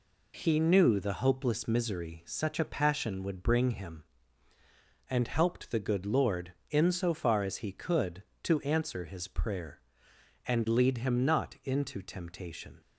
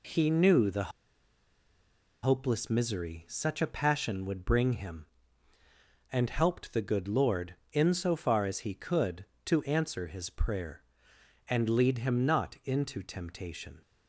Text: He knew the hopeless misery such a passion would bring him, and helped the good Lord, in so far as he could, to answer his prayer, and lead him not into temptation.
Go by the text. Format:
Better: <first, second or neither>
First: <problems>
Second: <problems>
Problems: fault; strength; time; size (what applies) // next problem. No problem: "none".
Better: first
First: none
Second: pauses between "the" and "hopeless"; strong; at 0.9 s; 1.3 s long